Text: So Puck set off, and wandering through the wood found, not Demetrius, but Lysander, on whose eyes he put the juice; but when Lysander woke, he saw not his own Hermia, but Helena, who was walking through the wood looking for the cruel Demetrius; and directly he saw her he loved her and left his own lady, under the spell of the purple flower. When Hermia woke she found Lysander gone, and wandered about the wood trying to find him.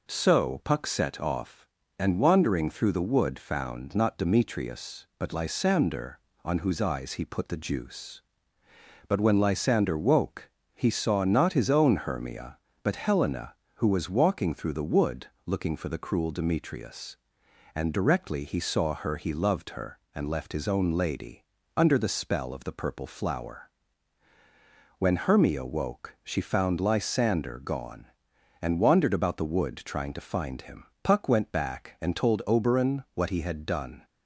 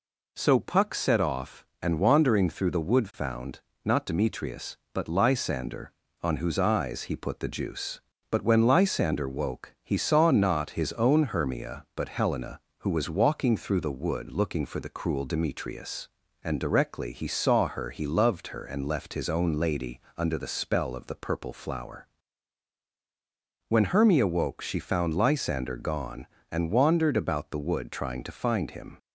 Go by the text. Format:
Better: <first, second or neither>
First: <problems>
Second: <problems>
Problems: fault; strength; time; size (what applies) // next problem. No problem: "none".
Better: second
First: pauses between "wood" and "looking"; slight; at 15.2 s; 0.20 s long // goes on to say "Puck went back and told Oberon what he had done"; strong; from 31.0 s on; 3.0 s long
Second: none